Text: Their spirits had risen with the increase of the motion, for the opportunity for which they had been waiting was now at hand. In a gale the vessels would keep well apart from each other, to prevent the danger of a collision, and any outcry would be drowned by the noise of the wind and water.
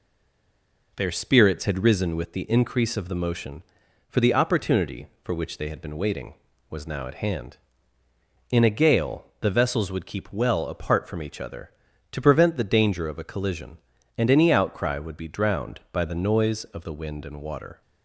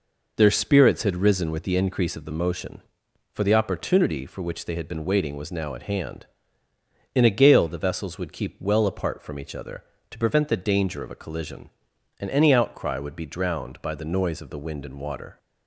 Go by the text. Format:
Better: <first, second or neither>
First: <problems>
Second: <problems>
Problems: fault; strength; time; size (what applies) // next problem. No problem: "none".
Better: second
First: stays silent before the first word; slight; until 0.9 s; 0.9 s long // pauses between "gale" and "the"; slight; at 9.2 s; 0.16 s long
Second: none